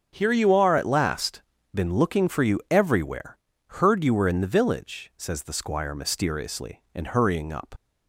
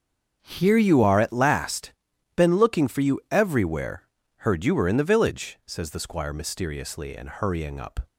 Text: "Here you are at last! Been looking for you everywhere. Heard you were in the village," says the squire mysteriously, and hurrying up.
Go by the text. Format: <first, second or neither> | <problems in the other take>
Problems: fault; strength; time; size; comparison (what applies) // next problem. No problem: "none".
second | starts louder than the rest; strong; until 1.1 s; 7.5 dB; also in the second // leaves "up" unfinished; at 7.7 s; 55 ms